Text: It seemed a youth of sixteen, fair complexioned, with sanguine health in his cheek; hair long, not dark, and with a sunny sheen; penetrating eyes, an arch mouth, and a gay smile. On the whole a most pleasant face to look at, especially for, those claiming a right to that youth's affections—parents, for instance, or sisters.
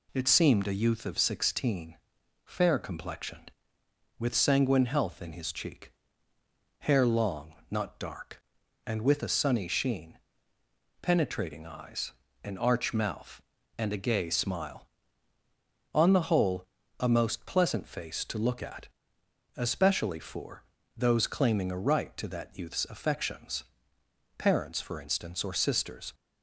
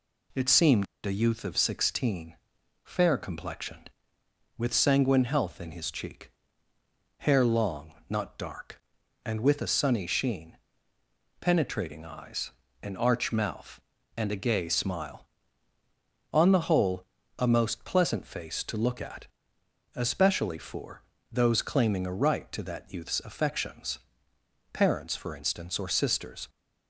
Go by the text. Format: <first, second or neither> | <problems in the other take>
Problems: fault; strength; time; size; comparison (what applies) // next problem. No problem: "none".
first | pauses between "seemed" and "a"; slight; at 0.8 s; 0.18 s long // pauses between "whole" and "a"; slight; at 17.0 s; 0.32 s long; slight in the first